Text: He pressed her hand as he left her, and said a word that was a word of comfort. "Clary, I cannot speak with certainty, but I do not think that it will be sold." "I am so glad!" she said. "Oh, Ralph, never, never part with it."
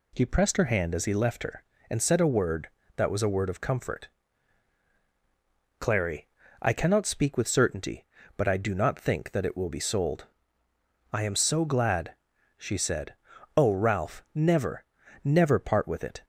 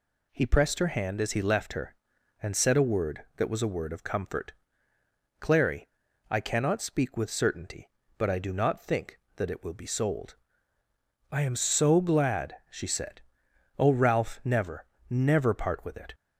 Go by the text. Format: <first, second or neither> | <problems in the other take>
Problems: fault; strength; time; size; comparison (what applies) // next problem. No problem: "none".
neither | none